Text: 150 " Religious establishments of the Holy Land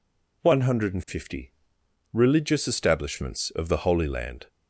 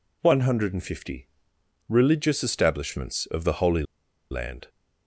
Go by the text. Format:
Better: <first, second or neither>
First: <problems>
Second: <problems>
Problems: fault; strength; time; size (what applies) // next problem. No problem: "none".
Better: first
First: none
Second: pauses between "Holy" and "Land"; noticeable; at 3.8 s; 0.47 s long